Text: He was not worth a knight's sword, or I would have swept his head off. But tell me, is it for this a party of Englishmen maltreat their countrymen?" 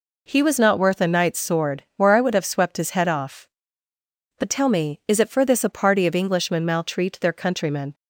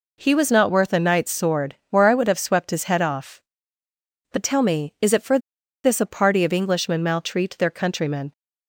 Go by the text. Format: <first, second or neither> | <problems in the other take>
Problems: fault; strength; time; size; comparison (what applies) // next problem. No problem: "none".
first | pauses between "for" and "this"; at 5.3 s; 0.45 s long